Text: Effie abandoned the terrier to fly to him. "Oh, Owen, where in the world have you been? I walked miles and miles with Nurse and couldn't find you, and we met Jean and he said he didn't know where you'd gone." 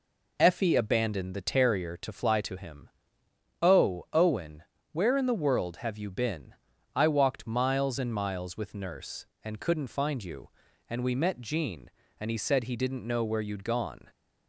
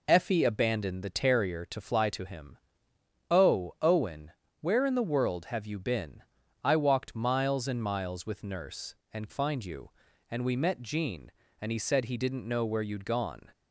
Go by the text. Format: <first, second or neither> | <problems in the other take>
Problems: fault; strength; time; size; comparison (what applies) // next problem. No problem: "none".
first | skips "couldn't"; at 9.2 s